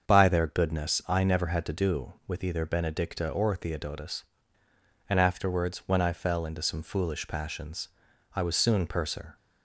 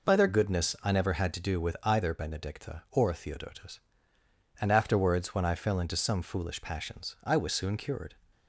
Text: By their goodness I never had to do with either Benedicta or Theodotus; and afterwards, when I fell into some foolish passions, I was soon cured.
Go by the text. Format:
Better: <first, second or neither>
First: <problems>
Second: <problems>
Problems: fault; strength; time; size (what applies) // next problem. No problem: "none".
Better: second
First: starts louder than the rest; until 1.1 s; 7 dB // says "purser" for "cured"; at 8.8 s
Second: none